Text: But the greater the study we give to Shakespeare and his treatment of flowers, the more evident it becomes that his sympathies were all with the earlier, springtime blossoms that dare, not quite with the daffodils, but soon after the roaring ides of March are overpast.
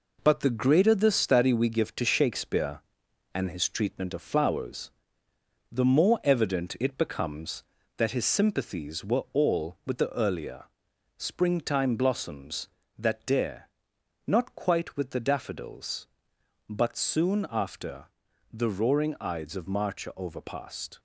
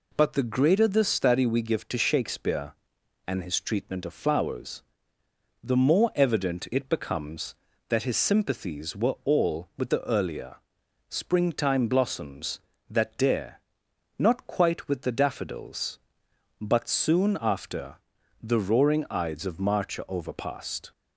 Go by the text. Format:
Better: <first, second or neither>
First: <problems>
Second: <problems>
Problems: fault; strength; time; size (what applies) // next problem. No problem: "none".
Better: second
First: gets quieter; noticeable; throughout; 6 dB // pauses between "after" and "the"; noticeable; at 18.0 s; 0.46 s long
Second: pauses between "after" and "the"; noticeable; at 17.9 s; 0.46 s long